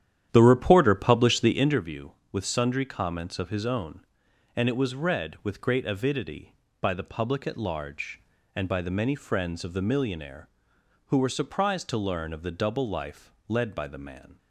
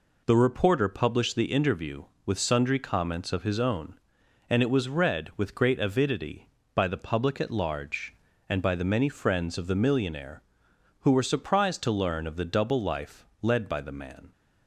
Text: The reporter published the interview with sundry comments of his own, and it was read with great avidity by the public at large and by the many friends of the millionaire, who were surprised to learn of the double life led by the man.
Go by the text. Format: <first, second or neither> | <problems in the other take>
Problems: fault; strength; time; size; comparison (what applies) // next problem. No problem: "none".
second | starts louder than the rest; strong; until 1.9 s; 10.5 dB // pauses between "life" and "led"; slight; at 13.3 s; 0.16 s long; slight in the second